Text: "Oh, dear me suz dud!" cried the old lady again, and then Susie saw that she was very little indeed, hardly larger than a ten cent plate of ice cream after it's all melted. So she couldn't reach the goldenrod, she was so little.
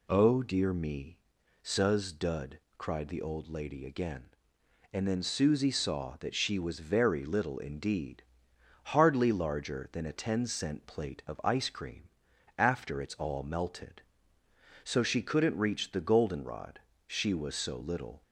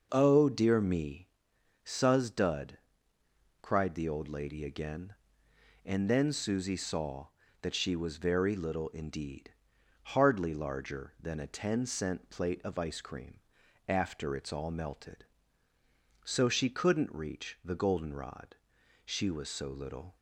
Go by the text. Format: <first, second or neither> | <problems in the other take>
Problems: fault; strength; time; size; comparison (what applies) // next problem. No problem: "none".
neither | pauses between "me" and "suz"; noticeable; the same in both // pauses between "cream" and "after"; noticeable; the same in both